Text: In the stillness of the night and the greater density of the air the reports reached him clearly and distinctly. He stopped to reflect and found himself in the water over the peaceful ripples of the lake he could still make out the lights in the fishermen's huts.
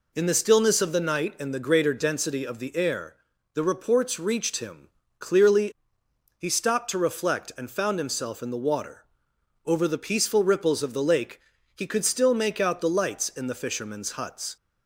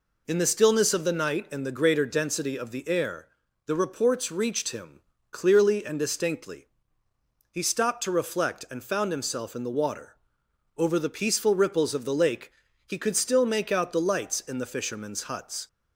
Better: second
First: pauses between "air" and "the"; at 3.1 s; 0.40 s long // pauses between "him" and "clearly"; slight; at 4.8 s; 0.28 s long // skips "and distinctly"; at 6.0 s // pauses between "water" and "over"; noticeable; at 9.0 s; 0.62 s long // pauses between "lake" and "he"; slight; at 11.4 s; 0.32 s long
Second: pauses between "air" and "the"; at 3.2 s; 0.40 s long // pauses between "him" and "clearly"; slight; at 5.0 s; 0.28 s long // pauses between "water" and "over"; noticeable; at 10.1 s; 0.62 s long // pauses between "lake" and "he"; slight; at 12.5 s; 0.32 s long

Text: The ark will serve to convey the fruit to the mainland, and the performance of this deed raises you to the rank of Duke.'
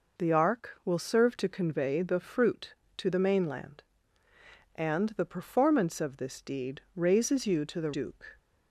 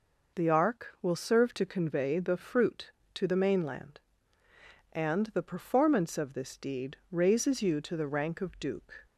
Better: second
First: skips "rank of"; at 7.9 s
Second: none

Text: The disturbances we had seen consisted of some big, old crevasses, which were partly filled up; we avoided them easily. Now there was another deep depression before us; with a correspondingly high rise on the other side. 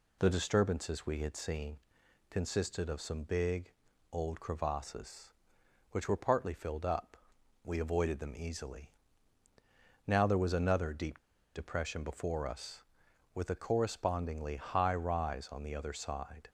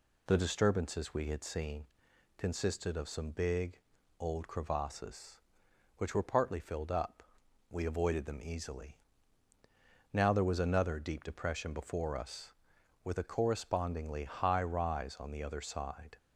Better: second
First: pauses between "seen" and "consisted"; noticeable; at 1.7 s; 0.52 s long // pauses between "deep" and "depression"; at 11.1 s; 0.36 s long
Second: pauses between "seen" and "consisted"; noticeable; at 1.8 s; 0.52 s long

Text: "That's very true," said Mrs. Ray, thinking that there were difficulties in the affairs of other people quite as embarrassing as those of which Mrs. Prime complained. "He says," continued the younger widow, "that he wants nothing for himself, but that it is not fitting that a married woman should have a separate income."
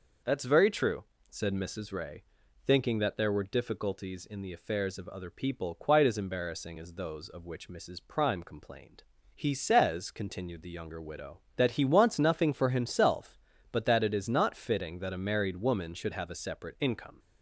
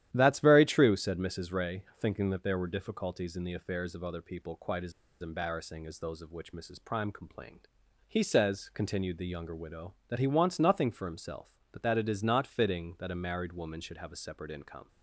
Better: first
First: none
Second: starts louder than the rest; strong; until 1.1 s; 12 dB // pauses between "as" and "embarrassing"; slight; at 4.9 s; 0.29 s long

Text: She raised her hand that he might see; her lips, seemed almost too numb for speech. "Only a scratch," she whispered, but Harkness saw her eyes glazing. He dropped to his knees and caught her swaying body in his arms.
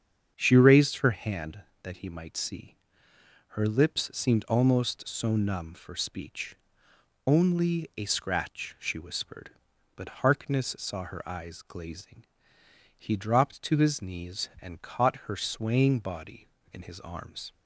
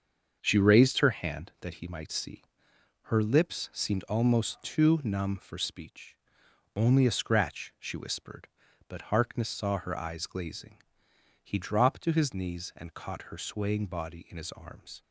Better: second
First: starts louder than the rest; strong; until 1.3 s; 7.5 dB // says "so" for "too"; at 5.0 s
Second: starts louder than the rest; until 1.4 s; 6.5 dB

